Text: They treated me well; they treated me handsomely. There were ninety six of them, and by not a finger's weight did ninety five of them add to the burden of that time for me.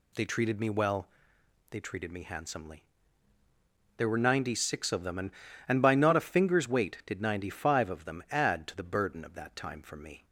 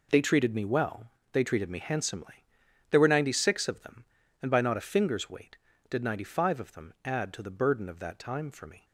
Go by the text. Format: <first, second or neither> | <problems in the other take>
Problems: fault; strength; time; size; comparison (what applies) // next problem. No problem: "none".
second | says "and" twice; at 5.6 s